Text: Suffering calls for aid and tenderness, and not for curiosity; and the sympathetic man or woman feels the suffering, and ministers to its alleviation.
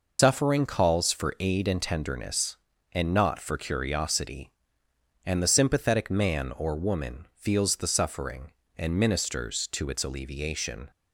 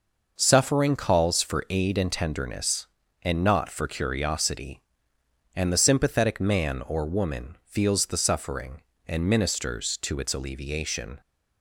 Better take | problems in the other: second | loses the start of "Suffering"; at 0.1 s; 115 ms

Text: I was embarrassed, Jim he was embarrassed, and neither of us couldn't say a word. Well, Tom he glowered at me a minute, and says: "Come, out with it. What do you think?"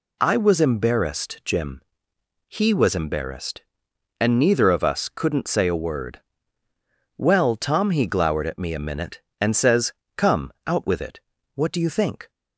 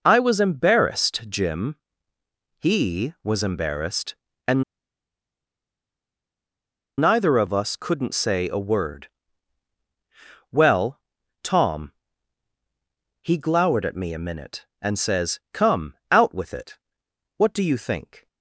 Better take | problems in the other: first | pauses between "Jim" and "he"; noticeable; at 1.7 s; 0.86 s long; noticeable in the first // pauses between "and" and "neither"; strong; at 4.6 s; 2.3 s long // pauses between "Tom" and "he"; strong; at 11.9 s; 1.3 s long

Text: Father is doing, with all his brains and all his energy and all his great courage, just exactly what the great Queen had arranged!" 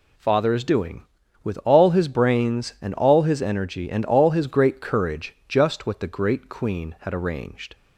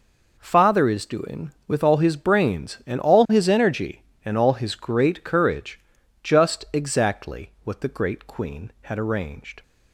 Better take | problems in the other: second | skips "exactly"; at 5.8 s

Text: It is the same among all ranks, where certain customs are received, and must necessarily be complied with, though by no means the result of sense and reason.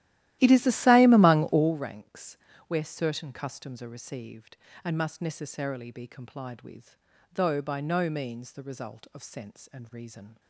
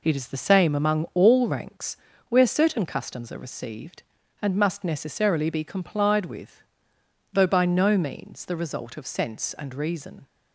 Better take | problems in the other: second | starts louder than the rest; strong; until 1.9 s; 14.5 dB

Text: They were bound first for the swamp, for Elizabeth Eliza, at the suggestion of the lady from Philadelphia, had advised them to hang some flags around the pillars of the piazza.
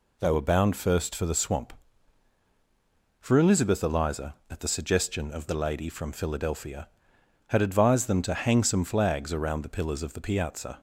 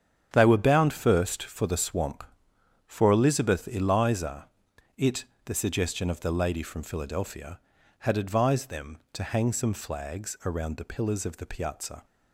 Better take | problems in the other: first | starts louder than the rest; strong; until 1.3 s; 8.5 dB // says "it" for "at"; at 4.9 s

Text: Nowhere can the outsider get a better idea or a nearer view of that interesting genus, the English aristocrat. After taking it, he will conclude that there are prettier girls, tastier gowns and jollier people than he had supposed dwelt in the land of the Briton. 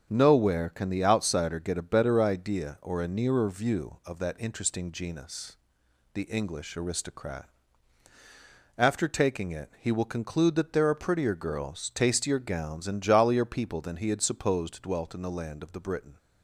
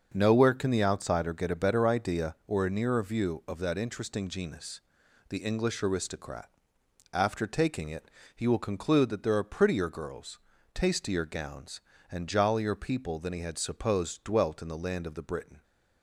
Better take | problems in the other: neither | starts louder than the rest; the same in both

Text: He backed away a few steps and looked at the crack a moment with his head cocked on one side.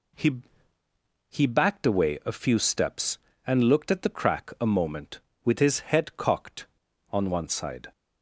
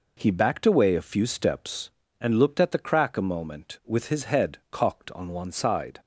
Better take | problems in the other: second | says "He" twice; at 1.2 s

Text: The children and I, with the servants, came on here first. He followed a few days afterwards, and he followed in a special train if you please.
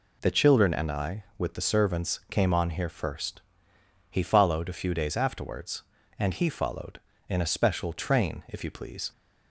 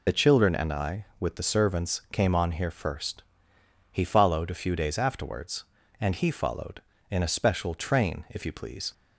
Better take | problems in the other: first | loses the start of "The"; at 0.0 s; 40 ms

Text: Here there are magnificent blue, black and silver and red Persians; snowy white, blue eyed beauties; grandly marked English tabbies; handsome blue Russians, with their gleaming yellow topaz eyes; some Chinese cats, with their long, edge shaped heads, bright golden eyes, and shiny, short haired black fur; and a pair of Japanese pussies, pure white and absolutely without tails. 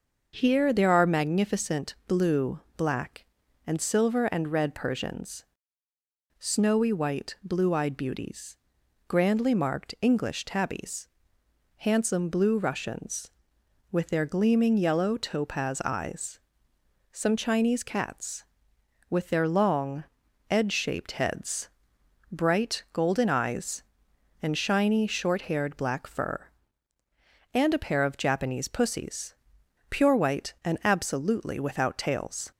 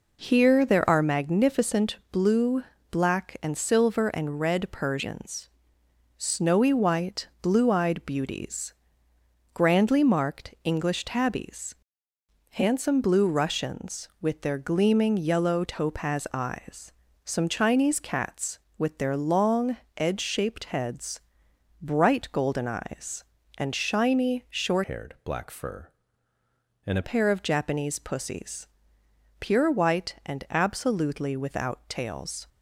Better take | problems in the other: first | pauses between "magnificent" and "blue"; slight; at 1.9 s; 0.16 s long // changes voice from "haired" to "a"; from 24.8 to 27.0 s; 2.2 s long

